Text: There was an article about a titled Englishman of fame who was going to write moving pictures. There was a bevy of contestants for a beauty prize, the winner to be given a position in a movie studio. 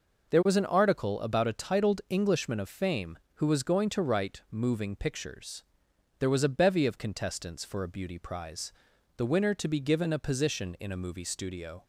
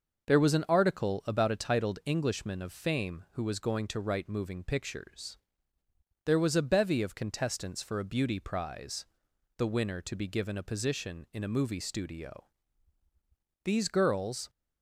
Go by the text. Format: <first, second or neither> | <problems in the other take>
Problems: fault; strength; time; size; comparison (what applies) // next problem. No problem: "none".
first | starts louder than the rest; noticeable; until 1.3 s; 6 dB // goes on to say "These girls"; noticeable; from 13.6 s on; 0.86 s long